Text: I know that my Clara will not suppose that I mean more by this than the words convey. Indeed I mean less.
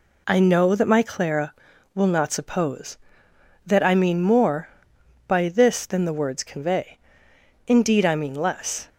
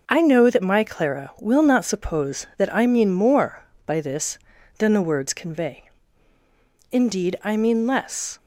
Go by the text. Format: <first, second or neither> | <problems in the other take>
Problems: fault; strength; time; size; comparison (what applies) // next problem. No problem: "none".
neither | none